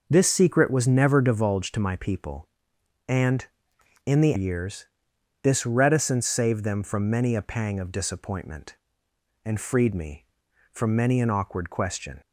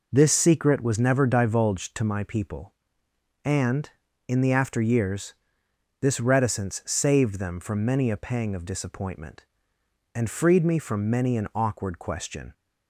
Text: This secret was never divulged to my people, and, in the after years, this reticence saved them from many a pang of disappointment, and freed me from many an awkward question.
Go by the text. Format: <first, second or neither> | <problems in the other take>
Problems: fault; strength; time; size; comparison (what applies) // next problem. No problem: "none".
second | skips "after"; at 4.3 s